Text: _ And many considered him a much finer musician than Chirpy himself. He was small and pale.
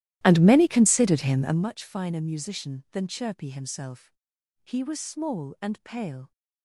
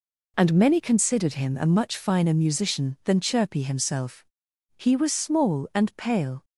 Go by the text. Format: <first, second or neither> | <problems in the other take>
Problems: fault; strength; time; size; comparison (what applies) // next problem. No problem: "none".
second | starts louder than the rest; strong; until 1.6 s; 14.5 dB